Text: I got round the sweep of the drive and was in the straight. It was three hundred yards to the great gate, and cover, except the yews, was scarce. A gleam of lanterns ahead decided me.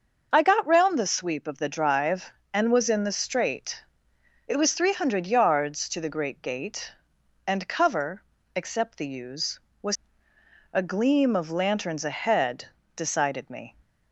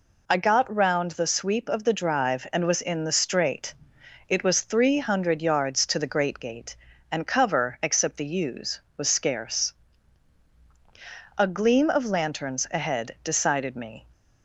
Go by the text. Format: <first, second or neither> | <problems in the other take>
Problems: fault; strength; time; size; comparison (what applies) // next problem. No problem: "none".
second | starts louder than the rest; until 1.3 s; 6.5 dB // skips "scarce"; at 10.3 s // pauses between "ahead" and "decided"; slight; at 12.6 s; 0.28 s long